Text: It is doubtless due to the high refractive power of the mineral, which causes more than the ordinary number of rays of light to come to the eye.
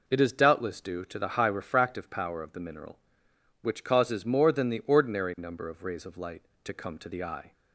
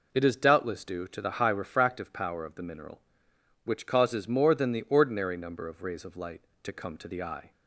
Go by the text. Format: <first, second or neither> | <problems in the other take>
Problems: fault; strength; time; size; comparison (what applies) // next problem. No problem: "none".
neither | none